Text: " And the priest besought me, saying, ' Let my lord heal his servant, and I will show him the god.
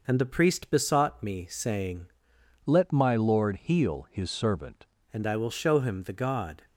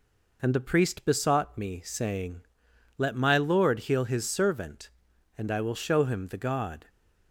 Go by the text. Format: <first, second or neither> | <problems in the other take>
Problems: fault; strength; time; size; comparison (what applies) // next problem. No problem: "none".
second | changes voice from "Let" to "servant"; from 2.6 to 4.8 s; 2.2 s long